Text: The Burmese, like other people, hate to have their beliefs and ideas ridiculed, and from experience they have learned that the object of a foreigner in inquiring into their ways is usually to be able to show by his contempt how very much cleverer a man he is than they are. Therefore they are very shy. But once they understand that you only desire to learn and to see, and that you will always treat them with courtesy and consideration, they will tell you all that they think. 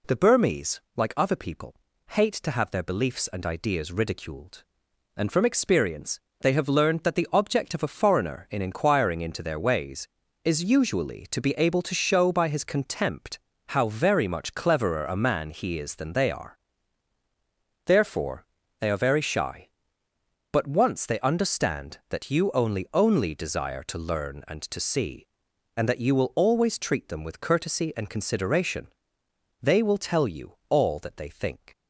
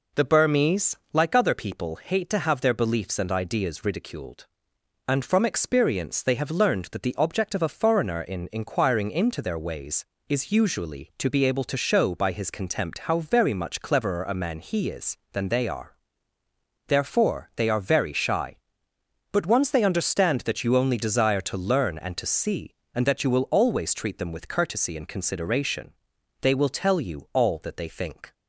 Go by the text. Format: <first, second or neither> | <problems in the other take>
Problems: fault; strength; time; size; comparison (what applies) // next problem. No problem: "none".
second | pauses between "experience" and "they"; slight; at 6.1 s; 0.22 s long // pauses between "contempt" and "how"; slight; at 13.3 s; 0.30 s long // pauses between "Therefore" and "they"; slight; at 18.4 s; 0.34 s long // says "only" twice; at 22.9 s // pauses between "you" and "all"; slight; at 30.5 s; 0.16 s long